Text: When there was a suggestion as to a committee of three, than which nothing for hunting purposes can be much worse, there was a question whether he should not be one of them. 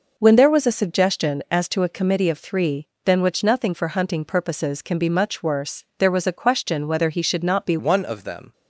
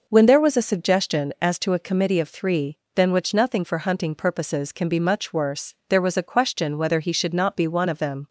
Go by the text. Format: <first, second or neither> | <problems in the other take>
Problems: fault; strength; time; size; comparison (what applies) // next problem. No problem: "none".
second | changes voice at "one"; from 7.7 s on; 0.8 s long